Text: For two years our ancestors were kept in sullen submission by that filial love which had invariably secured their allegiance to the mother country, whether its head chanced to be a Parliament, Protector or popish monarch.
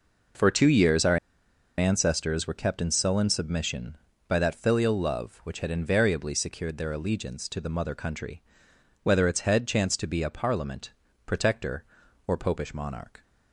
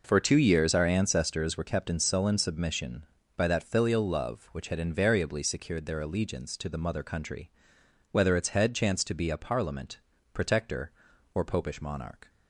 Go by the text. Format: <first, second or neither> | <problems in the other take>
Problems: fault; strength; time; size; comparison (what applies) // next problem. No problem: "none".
second | pauses between "our" and "ancestors"; noticeable; at 1.1 s; 0.61 s long